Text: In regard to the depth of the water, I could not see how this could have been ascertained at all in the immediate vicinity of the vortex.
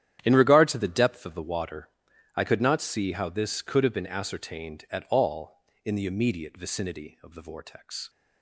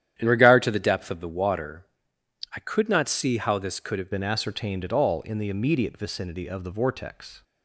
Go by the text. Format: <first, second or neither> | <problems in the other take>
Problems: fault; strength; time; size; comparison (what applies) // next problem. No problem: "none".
first | starts louder than the rest; strong; until 1.1 s; 10.5 dB; strong in the first // changes voice at "been"; from 4.1 s on; 3.3 s long